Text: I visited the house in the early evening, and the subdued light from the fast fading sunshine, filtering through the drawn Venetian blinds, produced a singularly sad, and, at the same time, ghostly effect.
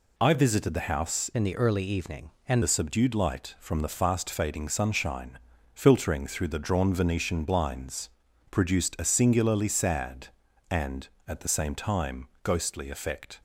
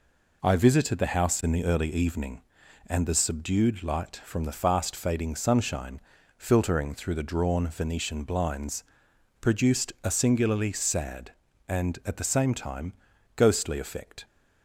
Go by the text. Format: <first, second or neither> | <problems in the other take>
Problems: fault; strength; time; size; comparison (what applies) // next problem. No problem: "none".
second | changes voice from "in" to "and"; from 1.3 to 2.6 s; 1.3 s long